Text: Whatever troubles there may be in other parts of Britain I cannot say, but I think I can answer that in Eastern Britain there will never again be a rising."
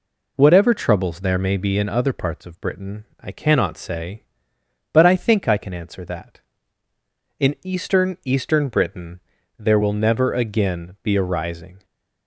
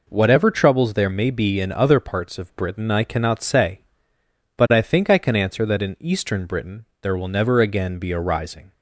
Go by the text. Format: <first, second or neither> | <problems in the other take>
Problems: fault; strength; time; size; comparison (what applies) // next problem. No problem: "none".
second | says "Eastern" twice; at 8.2 s // pauses between "Britain" and "there"; at 9.1 s; 0.38 s long; slight in the second